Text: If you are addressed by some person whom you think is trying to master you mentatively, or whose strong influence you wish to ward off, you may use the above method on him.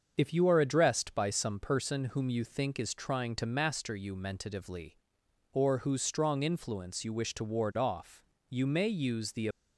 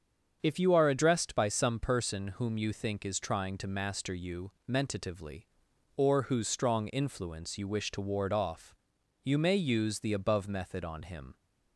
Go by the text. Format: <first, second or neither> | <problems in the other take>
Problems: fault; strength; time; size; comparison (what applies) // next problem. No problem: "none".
second | starts louder than the rest; until 1.2 s; 6.5 dB; strong in the second // stops before "above method on him"; at 9.5 s